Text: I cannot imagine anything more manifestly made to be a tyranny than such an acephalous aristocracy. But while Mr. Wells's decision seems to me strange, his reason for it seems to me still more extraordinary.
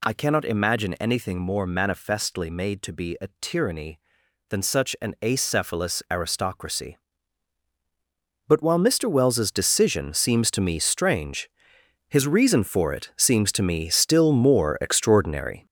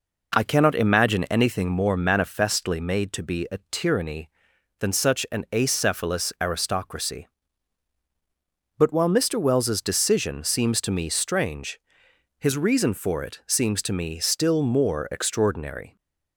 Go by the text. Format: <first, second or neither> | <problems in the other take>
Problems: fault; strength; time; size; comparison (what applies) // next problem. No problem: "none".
second | gets louder; noticeable; throughout; 6 dB